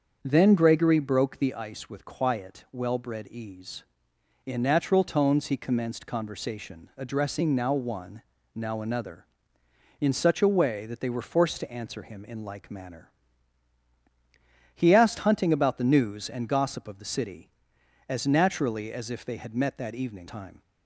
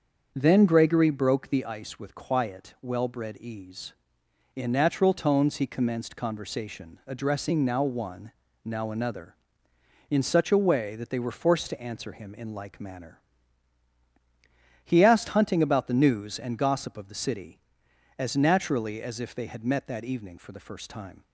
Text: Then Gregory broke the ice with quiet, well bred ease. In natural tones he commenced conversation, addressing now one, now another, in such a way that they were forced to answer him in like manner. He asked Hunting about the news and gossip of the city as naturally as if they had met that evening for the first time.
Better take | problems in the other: second | starts louder than the rest; until 1.2 s; 7 dB; also in the second // skips "for the first"; at 20.2 s

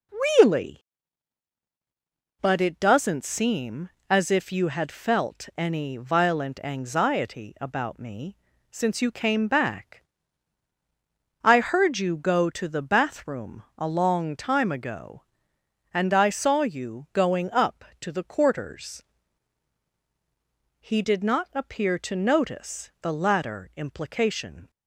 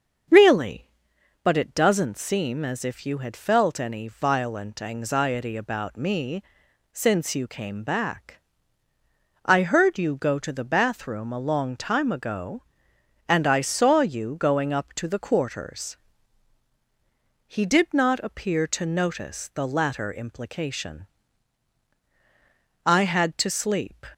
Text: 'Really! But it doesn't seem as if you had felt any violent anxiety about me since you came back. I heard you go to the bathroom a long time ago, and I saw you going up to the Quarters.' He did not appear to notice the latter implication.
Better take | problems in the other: first | starts louder than the rest; until 1.8 s; 6.5 dB // pauses between "me" and "since"; noticeable; at 6.4 s; 0.50 s long; slight in the first // goes on to say "I had to sleep"; noticeable; from 22.8 s on; 1.2 s long

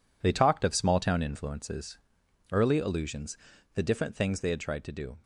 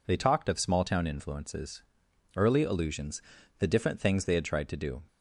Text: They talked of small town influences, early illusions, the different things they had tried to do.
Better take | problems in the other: second | gets quieter; strong; throughout; 8.5 dB

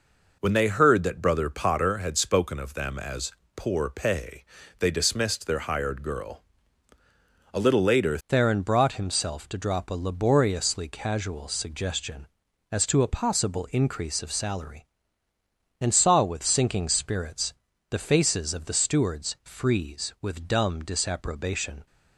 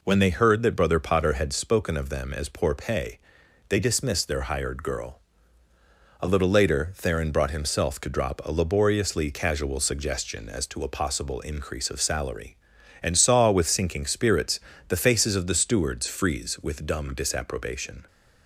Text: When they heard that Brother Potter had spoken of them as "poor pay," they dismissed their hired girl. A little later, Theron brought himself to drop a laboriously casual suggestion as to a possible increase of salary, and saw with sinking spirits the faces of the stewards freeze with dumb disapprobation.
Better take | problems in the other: second | pauses between "as" and "poor"; slight; at 3.3 s; 0.24 s long // changes voice at "Theron"; from 8.2 s on; 13.6 s long // pauses between "spirits" and "the"; slight; at 17.5 s; 0.36 s long; slight in the second

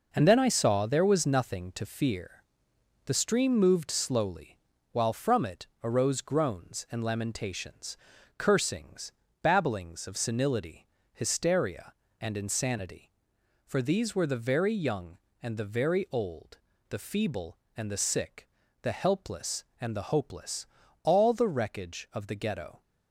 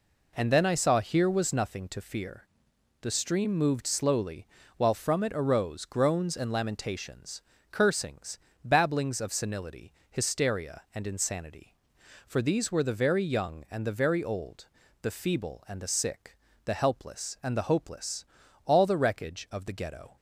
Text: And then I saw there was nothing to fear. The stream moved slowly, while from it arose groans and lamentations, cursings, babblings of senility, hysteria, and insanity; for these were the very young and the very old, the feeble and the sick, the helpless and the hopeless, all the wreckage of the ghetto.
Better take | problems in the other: first | says "here" for "there"; at 1.0 s

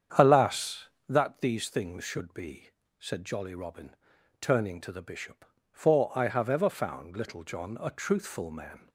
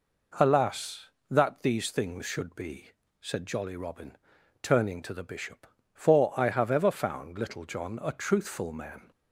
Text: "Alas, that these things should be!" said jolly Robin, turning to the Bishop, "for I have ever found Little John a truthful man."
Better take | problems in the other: second | starts louder than the rest; strong; until 1.1 s; 8.5 dB

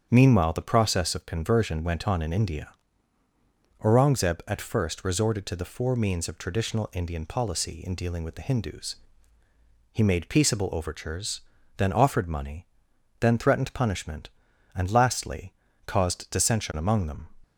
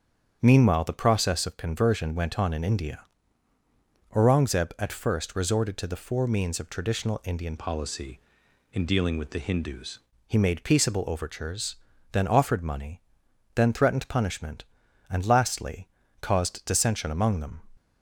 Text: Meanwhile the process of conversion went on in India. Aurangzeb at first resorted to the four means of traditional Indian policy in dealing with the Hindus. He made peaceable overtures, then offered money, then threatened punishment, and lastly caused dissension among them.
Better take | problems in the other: first | starts louder than the rest; strong; until 1.4 s; 8 dB; strong in the first // changes voice from "policy" to "Hindus"; from 7.5 to 9.9 s; 2.4 s long // pauses between "lastly" and "caused"; slight; at 15.8 s; 0.34 s long; slight in the first

